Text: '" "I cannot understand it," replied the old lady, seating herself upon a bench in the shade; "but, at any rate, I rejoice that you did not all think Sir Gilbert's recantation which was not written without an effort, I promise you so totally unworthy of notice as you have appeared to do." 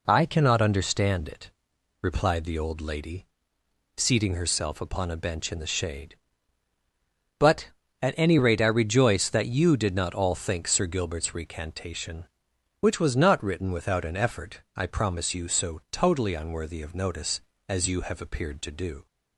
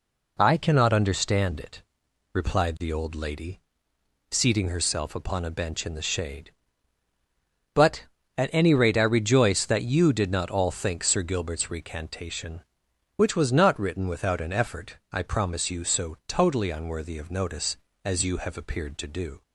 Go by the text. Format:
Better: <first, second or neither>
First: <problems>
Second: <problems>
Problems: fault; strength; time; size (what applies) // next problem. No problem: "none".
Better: neither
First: none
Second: none